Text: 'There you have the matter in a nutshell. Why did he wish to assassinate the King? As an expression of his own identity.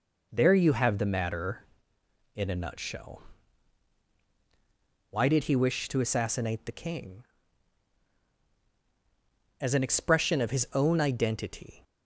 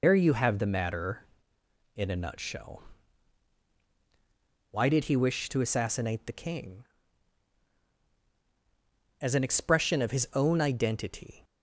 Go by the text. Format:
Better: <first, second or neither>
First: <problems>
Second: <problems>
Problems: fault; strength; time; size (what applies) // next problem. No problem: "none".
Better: first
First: none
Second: loses the start of "There"; at 0.0 s; 115 ms